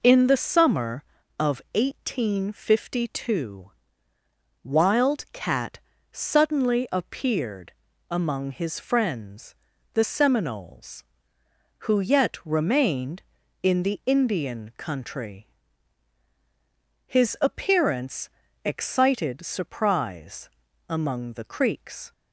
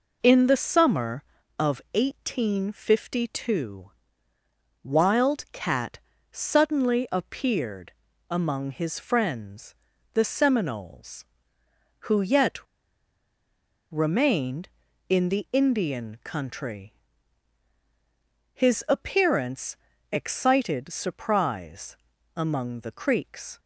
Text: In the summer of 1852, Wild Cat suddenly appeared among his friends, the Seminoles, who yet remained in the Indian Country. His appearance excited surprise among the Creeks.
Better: first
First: pauses between "Cat" and "suddenly"; slight; at 5.7 s; 0.32 s long // pauses between "appeared" and "among"; at 7.7 s; 0.38 s long // pauses between "appearance" and "excited"; slight; at 18.2 s; 0.34 s long // pauses between "surprise" and "among"; at 20.4 s; 0.40 s long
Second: pauses between "Cat" and "suddenly"; slight; at 5.9 s; 0.32 s long // pauses between "appeared" and "among"; at 7.9 s; 0.38 s long // pauses between "yet" and "remained"; strong; at 12.5 s; 1.3 s long // pauses between "appearance" and "excited"; slight; at 19.7 s; 0.34 s long // pauses between "surprise" and "among"; at 21.9 s; 0.40 s long

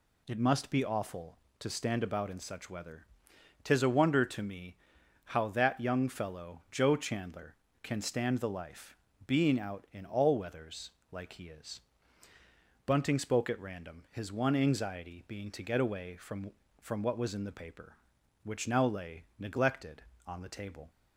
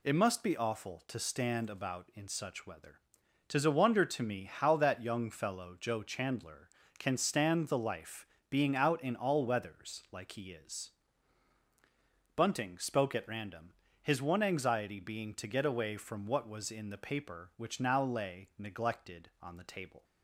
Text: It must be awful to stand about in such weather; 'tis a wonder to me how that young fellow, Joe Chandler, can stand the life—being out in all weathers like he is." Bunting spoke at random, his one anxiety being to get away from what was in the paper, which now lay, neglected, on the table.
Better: second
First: pauses between "me" and "how"; noticeable; at 4.7 s; 0.52 s long // pauses between "weathers" and "like"; slight; at 10.9 s; 0.22 s long // says "from" twice; at 16.8 s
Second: none

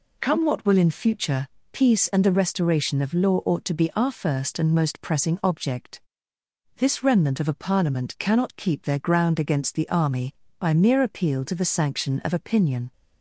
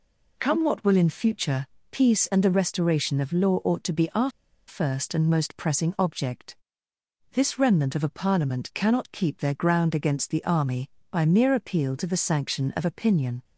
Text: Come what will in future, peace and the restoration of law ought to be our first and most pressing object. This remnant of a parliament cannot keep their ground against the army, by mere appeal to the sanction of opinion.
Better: first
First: none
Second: pauses between "our" and "first"; at 4.2 s; 0.38 s long

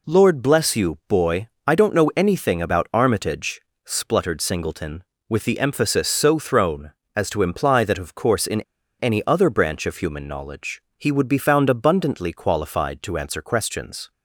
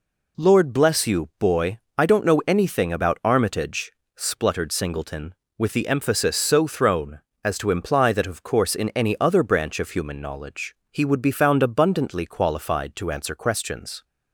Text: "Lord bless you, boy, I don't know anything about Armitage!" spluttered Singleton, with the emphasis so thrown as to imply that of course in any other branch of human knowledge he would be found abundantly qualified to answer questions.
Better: second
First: pauses between "in" and "any"; at 8.5 s; 0.39 s long // pauses between "knowledge" and "he"; slight; at 10.8 s; 0.16 s long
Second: pauses between "knowledge" and "he"; slight; at 10.7 s; 0.16 s long

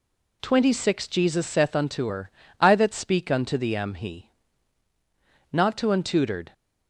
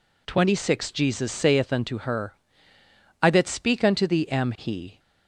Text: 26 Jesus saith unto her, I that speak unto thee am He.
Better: second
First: goes on to say "Not to untutored"; noticeable; from 5.5 s on; 1.0 s long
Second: none

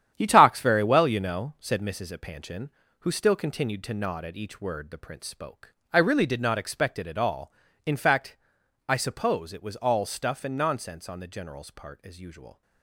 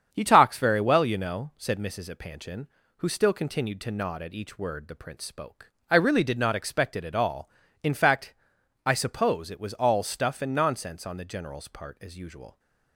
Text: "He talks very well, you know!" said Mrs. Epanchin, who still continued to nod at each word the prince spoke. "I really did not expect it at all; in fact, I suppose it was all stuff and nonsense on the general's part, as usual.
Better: second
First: gets quieter; strong; throughout; 9.5 dB // starts louder than the rest; strong; until 1.1 s; 10 dB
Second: starts louder than the rest; strong; until 1.1 s; 8 dB

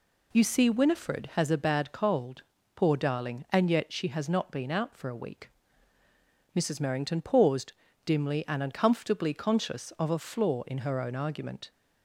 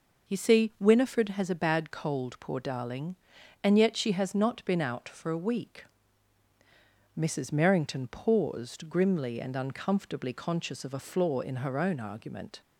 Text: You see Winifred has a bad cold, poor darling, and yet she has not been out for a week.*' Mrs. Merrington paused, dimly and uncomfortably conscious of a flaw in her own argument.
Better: first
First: none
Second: says "grimly" for "dimly"; at 8.8 s

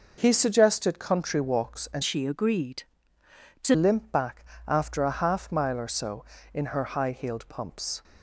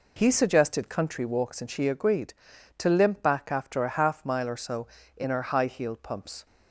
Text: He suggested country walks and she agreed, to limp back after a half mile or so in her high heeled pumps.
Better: second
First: changes voice from "she" to "to"; from 2.0 to 3.7 s; 1.7 s long // pauses between "back" and "after"; slight; at 4.4 s; 0.24 s long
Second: none

